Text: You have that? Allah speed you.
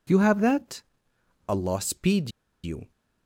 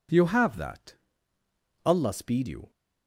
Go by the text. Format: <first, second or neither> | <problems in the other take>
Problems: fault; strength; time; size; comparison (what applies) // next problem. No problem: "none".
second | pauses between "speed" and "you"; slight; at 2.3 s; 0.33 s long